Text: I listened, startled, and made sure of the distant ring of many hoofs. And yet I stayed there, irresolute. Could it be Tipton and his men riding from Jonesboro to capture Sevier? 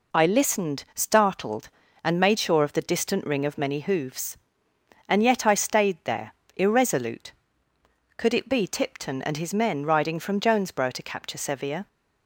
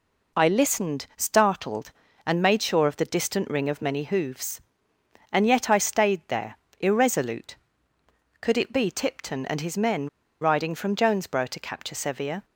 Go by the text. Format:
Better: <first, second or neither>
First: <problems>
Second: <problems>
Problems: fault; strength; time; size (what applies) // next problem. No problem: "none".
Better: first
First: none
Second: pauses between "men" and "riding"; slight; at 10.0 s; 0.32 s long